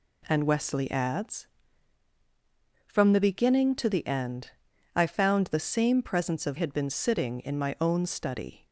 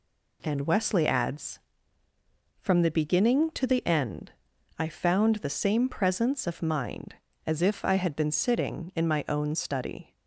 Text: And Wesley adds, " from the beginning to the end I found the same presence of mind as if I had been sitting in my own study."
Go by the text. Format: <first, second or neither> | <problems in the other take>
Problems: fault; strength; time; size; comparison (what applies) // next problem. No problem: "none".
second | pauses between "end" and "I"; at 4.5 s; 0.44 s long; noticeable in the second // skips "mind as if I"; at 6.5 s